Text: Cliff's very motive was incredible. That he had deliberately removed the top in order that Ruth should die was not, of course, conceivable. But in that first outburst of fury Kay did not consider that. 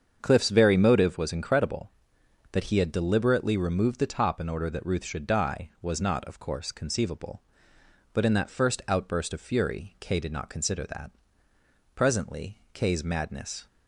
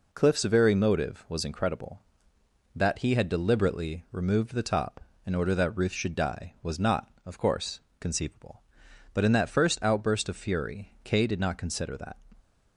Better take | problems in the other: second | starts louder than the rest; strong; until 1.2 s; 7.5 dB // goes on to say "Presently Kay's madness"; strong; from 11.9 s on; 1.7 s long

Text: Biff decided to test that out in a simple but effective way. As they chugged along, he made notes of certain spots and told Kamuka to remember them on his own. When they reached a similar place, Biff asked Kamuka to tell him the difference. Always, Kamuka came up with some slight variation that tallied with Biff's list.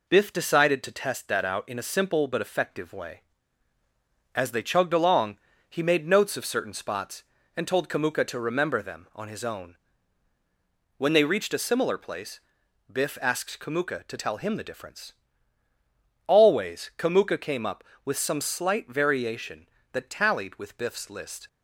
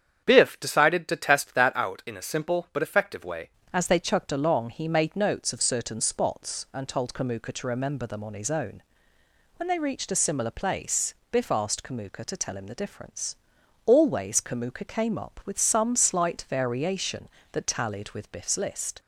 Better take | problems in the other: first | starts louder than the rest; strong; until 1.2 s; 8 dB // changes voice at "As"; from 3.7 s on; 15.3 s long

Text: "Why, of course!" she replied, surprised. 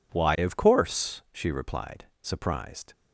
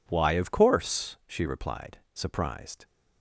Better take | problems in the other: neither | none

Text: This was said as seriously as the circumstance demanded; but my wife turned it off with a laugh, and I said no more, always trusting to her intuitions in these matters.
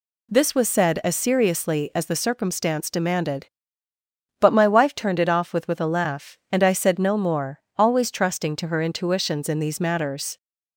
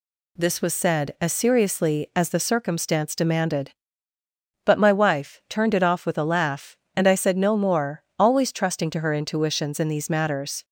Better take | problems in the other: second | says "with" twice; at 5.6 s

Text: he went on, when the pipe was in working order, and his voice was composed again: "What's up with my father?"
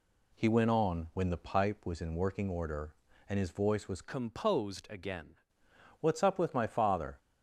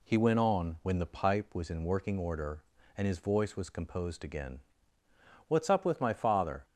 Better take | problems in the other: second | changes voice from "composed" to "again"; from 4.0 to 5.3 s; 1.3 s long

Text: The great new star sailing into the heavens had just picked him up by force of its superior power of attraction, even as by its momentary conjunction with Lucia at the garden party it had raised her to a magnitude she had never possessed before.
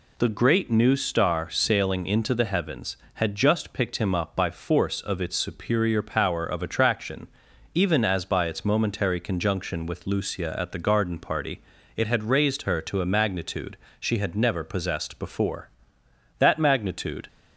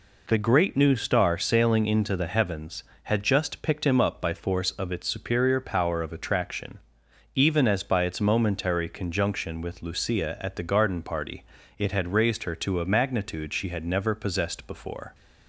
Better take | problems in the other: second | pauses between "party" and "it"; at 11.5 s; 0.38 s long; slight in the second // pauses between "magnitude" and "she"; slight; at 13.7 s; 0.24 s long // goes on to say "That magnitude"; noticeable; from 16.3 s on; 0.88 s long

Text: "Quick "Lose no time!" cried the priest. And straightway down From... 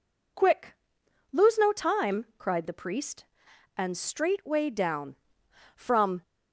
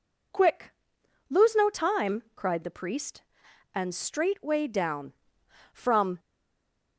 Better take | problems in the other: first | pauses between "Quick" and "Lose"; noticeable; at 0.7 s; 0.58 s long; noticeable in the first // stays silent after the last word; slight; from 6.1 s on; 0.8 s long

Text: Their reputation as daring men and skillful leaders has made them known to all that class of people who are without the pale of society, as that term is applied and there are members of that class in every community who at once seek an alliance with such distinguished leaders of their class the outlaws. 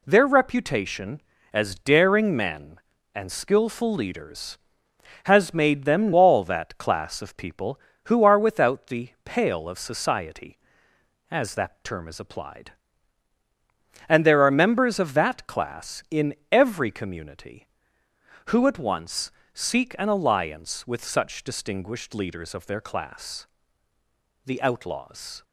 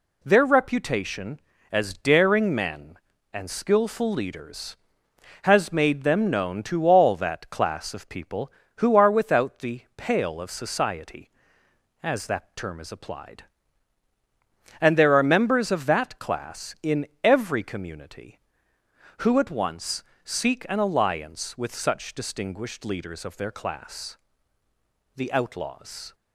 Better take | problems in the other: second | skips "known to"; at 6.1 s // pauses between "in" and "every"; slight; at 16.3 s; 0.18 s long; slight in the second // pauses between "once" and "seek"; slight; at 19.2 s; 0.24 s long; slight in the second // pauses between "class" and "the"; noticeable; at 23.4 s; 0.98 s long; noticeable in the second

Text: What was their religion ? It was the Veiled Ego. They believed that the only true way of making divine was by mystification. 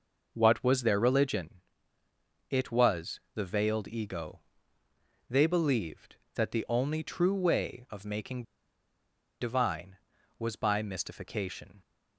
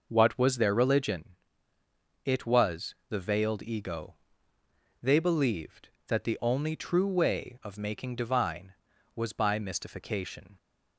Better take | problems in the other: second | pauses between "making" and "divine"; at 8.4 s; 0.98 s long

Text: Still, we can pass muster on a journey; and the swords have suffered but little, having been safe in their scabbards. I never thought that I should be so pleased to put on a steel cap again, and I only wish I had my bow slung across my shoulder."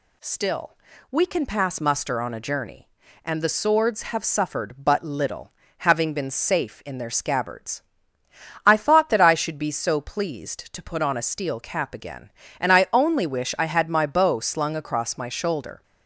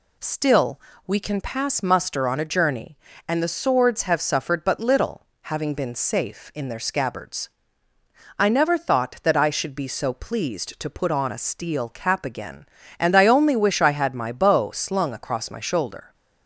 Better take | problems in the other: second | skips "never"; at 8.7 s

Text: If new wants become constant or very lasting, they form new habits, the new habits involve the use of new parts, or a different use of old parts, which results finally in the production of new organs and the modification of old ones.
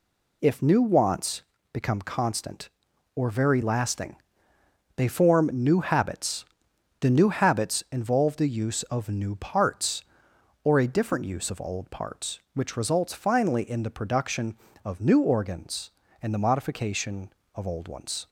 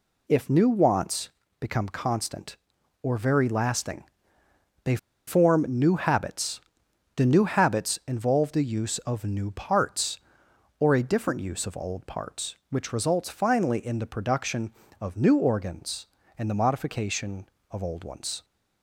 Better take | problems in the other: first | pauses between "wants" and "become"; slight; at 1.2 s; 0.32 s long; slight in the first // pauses between "they" and "form"; slight; at 4.9 s; 0.30 s long

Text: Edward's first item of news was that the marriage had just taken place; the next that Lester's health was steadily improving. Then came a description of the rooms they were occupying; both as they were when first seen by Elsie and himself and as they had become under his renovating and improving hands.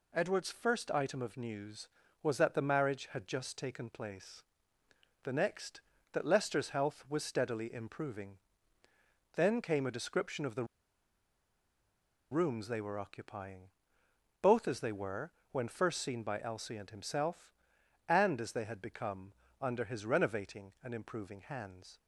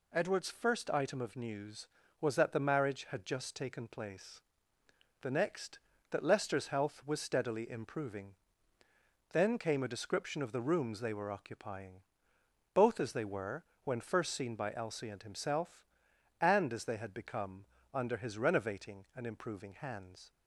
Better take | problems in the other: second | pauses between "the" and "rooms"; strong; at 10.6 s; 1.6 s long // pauses between "were" and "when"; slight; at 15.3 s; 0.20 s long; slight in the second // pauses between "become" and "under"; slight; at 19.3 s; 0.28 s long; slight in the second

